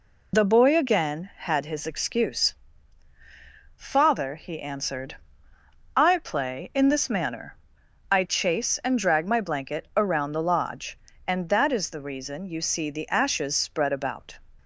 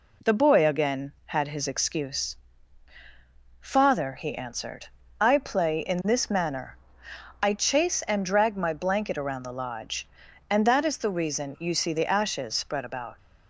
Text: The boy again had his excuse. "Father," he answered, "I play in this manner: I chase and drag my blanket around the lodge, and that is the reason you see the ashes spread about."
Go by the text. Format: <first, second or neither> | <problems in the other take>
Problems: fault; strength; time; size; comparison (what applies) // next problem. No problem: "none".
second | loses the start of "The"; at 0.3 s; 50 ms